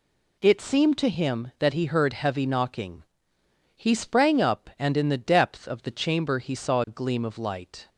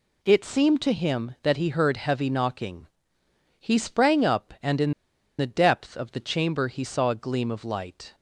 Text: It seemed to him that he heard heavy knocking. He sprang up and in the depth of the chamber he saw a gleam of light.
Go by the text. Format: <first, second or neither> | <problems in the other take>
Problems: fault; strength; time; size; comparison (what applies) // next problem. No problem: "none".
first | pauses between "in" and "the"; noticeable; at 4.9 s; 0.47 s long